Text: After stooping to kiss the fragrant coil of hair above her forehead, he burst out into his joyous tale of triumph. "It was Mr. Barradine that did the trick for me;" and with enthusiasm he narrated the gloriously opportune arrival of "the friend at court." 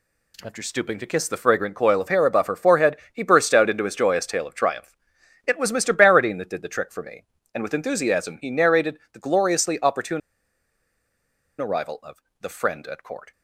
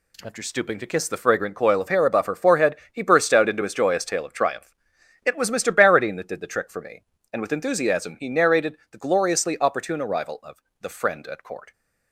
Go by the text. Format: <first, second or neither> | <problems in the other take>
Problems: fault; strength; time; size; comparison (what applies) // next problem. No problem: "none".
second | pauses between "opportune" and "arrival"; strong; at 10.2 s; 1.3 s long // pauses between "of" and "the"; slight; at 12.2 s; 0.18 s long; slight in the second